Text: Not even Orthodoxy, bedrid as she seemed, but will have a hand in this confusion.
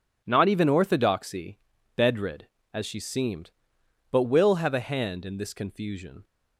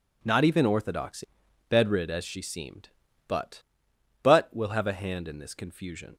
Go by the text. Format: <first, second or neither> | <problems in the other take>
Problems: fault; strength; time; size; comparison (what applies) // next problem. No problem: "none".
first | says "but" twice; at 4.2 s